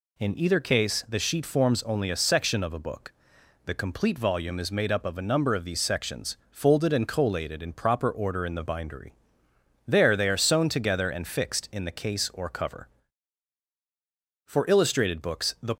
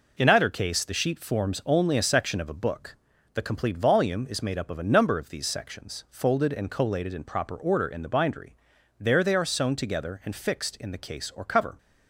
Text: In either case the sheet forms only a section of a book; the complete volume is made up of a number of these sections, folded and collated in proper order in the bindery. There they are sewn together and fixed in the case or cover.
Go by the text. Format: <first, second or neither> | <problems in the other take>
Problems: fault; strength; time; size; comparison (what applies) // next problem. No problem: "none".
second | goes on to say "For illustrated books the"; noticeable; from 14.4 s on; 1.3 s long